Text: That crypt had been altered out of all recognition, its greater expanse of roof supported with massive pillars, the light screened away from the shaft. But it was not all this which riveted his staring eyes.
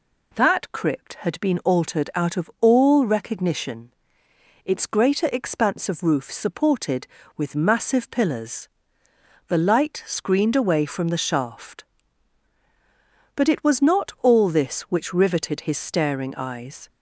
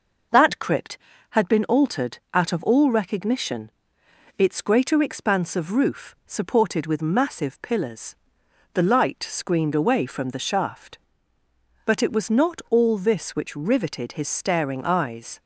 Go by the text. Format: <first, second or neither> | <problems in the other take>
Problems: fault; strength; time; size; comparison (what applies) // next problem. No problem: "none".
neither | none